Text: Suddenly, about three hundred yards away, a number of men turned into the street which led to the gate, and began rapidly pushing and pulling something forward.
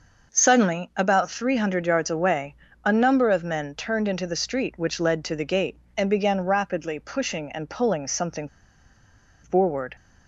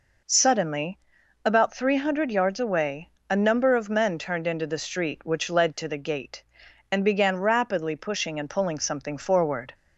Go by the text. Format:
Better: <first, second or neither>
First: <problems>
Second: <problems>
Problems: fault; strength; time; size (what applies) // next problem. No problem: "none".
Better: second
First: starts louder than the rest; noticeable; until 1.3 s; 6 dB // pauses between "something" and "forward"; noticeable; at 8.4 s; 0.96 s long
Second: none